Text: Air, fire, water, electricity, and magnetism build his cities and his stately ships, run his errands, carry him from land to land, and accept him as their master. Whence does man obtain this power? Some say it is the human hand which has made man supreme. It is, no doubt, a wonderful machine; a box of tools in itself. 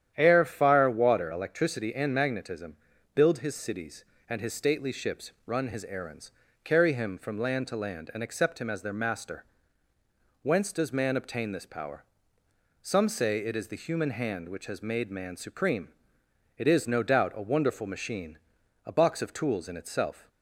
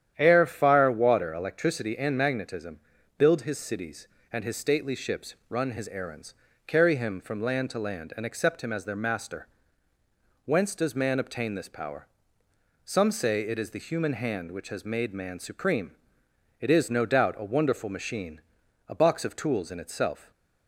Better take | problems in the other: neither | starts louder than the rest; strong; the same in both // pauses between "magnetism" and "build"; the same in both

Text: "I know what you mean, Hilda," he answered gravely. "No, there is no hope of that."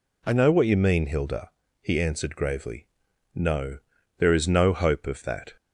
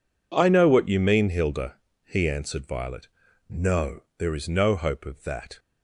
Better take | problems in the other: first | says "violet" for "gravely"; at 2.6 s

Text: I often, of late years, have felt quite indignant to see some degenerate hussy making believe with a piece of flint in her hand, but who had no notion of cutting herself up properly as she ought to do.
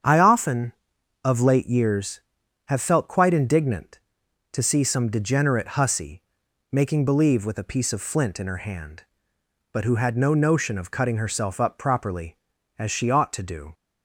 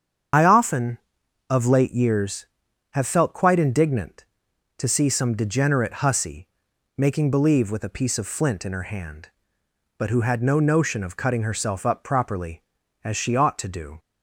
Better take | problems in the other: first | loses the start of "I"; at 0.3 s; 40 ms // starts louder than the rest; strong; until 1.8 s; 8 dB; strong in the first // pauses between "hussy" and "making"; noticeable; at 6.4 s; 0.50 s long; noticeable in the first

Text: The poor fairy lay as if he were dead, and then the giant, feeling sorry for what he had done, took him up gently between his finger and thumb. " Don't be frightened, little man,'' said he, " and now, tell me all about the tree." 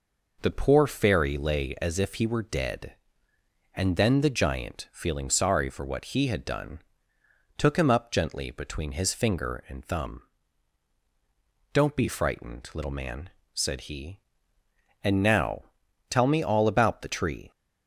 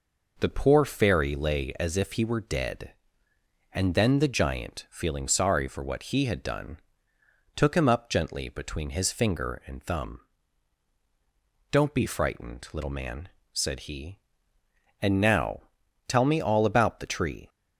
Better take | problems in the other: neither | none

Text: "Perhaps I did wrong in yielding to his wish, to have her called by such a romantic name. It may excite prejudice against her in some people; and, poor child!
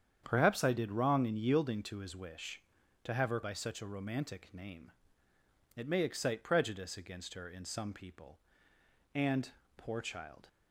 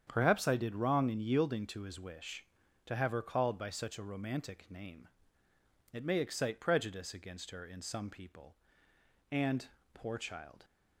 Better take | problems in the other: second | starts louder than the rest; strong; until 1.2 s; 8.5 dB; strong in the second // skips "called"; at 3.4 s

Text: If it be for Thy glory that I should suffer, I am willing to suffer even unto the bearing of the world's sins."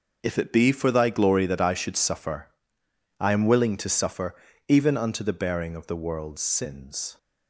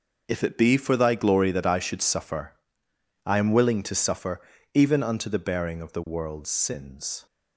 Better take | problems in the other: neither | pauses between "suffer" and "even"; slight; the same in both

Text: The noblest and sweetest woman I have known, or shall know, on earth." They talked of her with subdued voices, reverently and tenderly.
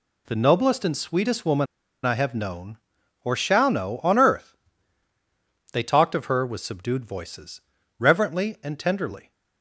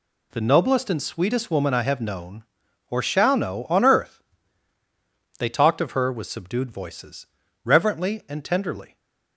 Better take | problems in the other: second | pauses between "woman" and "I"; at 1.6 s; 0.39 s long

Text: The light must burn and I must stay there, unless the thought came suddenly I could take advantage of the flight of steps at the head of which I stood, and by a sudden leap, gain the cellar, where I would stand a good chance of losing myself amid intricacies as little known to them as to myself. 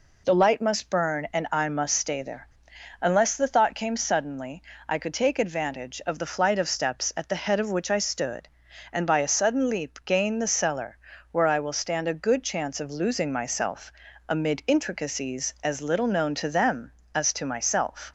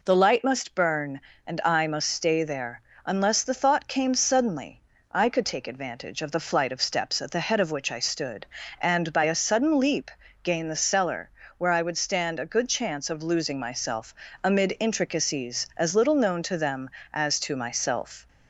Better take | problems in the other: second | pauses between "suddenly" and "I"; slight; at 4.5 s; 0.28 s long; slight in the second // says "will" for "would"; at 11.5 s // pauses between "myself" and "amid"; slight; at 13.9 s; 0.36 s long; slight in the second

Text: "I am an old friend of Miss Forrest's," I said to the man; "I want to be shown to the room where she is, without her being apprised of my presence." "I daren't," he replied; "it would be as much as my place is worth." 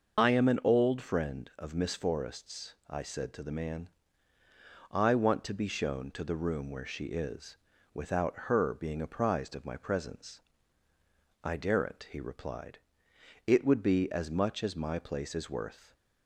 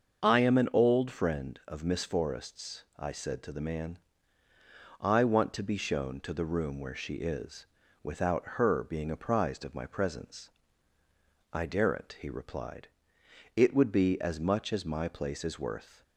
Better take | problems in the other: second | loses the start of "I"; at 0.1 s; 45 ms // starts louder than the rest; noticeable; until 1.2 s; 6 dB; also in the second

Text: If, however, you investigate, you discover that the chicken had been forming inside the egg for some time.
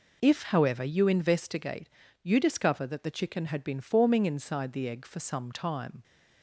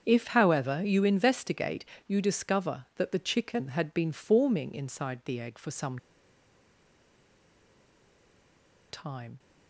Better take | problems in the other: first | starts louder than the rest; strong; until 1.0 s; 7.5 dB // pauses between "some" and "time"; strong; at 5.9 s; 2.9 s long

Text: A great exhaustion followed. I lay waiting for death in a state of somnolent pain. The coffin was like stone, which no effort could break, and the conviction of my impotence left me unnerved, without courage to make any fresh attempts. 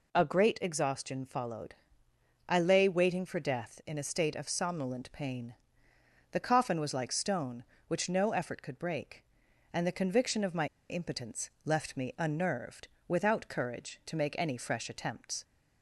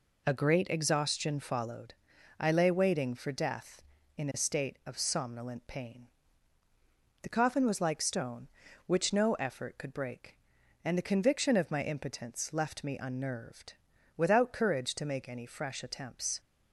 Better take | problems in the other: second | pauses between "my" and "impotence"; slight; at 10.6 s; 0.23 s long // pauses between "impotence" and "left"; slight; at 11.4 s; 0.16 s long

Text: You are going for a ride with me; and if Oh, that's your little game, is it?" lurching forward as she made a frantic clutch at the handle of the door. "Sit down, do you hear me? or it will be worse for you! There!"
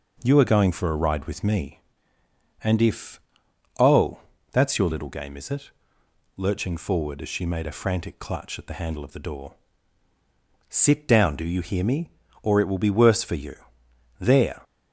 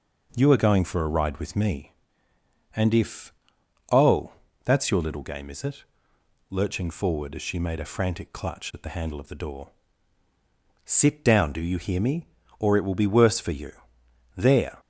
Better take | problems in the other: neither | pauses between "if" and "Oh"; noticeable; the same in both

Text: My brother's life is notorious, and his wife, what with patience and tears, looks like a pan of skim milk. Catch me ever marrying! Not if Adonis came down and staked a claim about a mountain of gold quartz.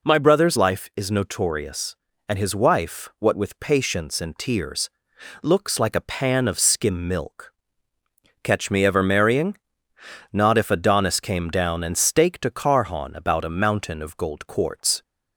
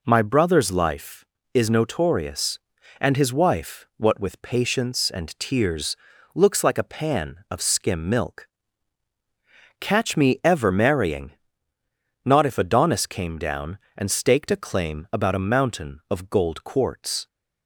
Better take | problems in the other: second | says "carhon" for "claim"; at 12.4 s

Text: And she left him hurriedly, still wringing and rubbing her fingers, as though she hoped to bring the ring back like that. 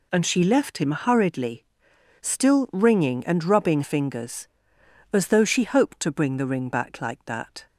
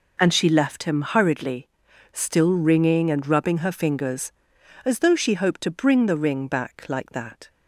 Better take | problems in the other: second | skips "her"; at 3.8 s

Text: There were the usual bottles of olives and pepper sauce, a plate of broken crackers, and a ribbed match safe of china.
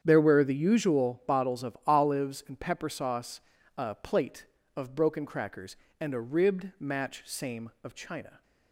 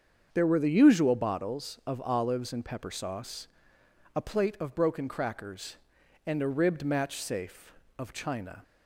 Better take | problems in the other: second | starts louder than the rest; strong; until 1.0 s; 8.5 dB; also in the second // says "same" for "safe"; at 7.2 s

